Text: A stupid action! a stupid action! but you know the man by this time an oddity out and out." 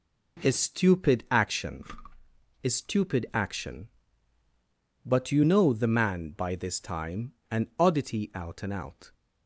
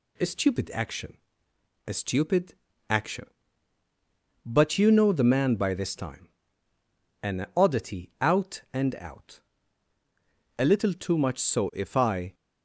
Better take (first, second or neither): first